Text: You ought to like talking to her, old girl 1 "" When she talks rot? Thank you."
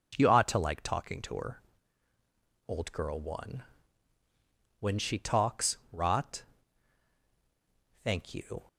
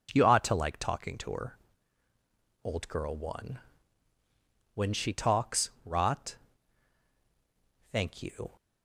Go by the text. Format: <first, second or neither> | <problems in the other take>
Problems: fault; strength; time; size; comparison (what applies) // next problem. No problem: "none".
neither | none